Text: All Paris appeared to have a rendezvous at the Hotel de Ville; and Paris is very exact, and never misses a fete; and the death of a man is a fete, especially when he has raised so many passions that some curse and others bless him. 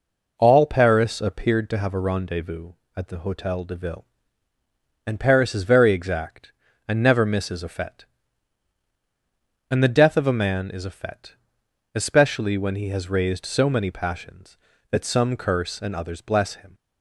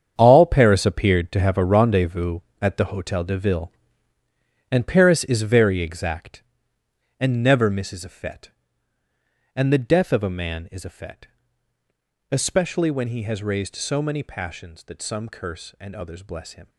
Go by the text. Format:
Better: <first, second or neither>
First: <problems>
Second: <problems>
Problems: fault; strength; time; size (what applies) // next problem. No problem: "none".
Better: first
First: none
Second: gets quieter; strong; throughout; 12 dB